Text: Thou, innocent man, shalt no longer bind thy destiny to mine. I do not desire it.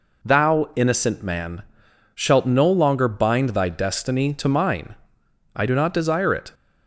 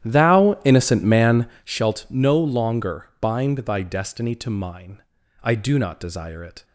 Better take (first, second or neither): first